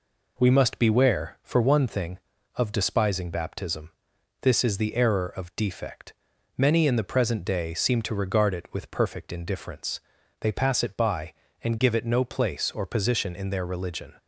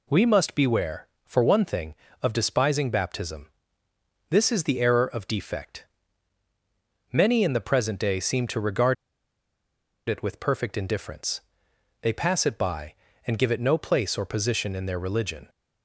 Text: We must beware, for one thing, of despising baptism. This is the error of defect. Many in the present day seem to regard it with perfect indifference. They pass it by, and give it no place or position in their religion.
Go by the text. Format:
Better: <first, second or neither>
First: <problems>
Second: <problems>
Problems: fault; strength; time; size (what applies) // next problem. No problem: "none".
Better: first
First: none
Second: pauses between "regard" and "it"; at 8.9 s; 1.1 s long